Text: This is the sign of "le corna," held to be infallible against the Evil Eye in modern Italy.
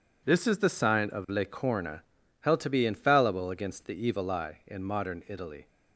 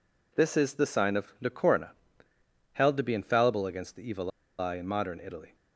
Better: first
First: none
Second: pauses between "Evil" and "Eye"; slight; at 4.3 s; 0.28 s long

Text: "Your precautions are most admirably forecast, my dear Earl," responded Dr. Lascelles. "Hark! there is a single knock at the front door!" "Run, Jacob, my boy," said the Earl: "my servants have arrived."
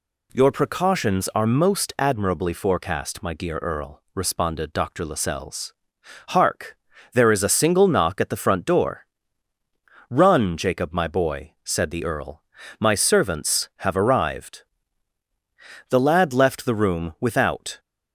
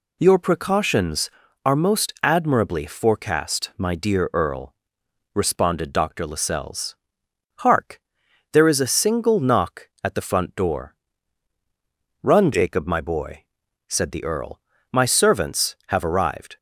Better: second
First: goes on to say "The lad left the room without"; strong; from 15.8 s on; 1.9 s long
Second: none

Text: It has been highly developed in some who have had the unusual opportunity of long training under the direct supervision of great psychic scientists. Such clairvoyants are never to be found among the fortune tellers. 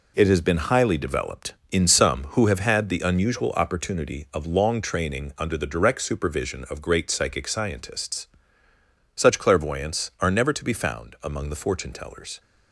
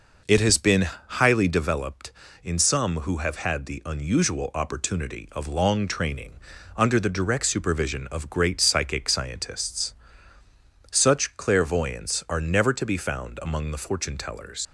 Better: first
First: none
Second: pauses between "been" and "highly"; slight; at 0.8 s; 0.20 s long // pauses between "training" and "under"; at 6.3 s; 0.44 s long // leaves "tellers" unfinished; at 14.6 s; 85 ms

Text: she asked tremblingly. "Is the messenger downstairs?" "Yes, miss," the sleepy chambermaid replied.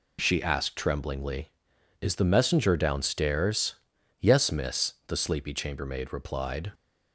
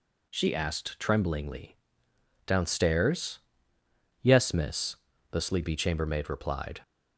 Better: first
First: none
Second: skips "Is the messenger"; at 2.1 s

